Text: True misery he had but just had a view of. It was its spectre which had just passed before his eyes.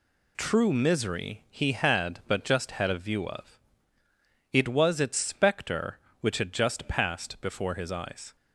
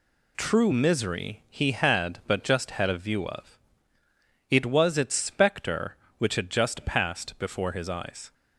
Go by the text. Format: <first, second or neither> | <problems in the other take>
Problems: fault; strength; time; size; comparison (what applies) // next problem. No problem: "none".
neither | none